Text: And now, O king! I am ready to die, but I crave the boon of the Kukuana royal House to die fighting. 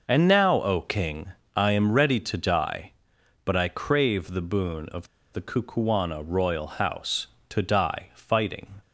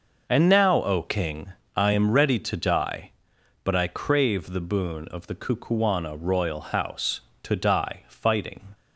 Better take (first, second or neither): second